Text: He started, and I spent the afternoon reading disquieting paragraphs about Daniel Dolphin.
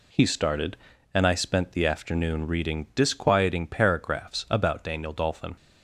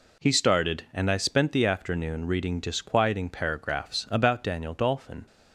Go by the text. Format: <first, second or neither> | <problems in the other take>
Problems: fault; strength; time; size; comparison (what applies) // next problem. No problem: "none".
neither | none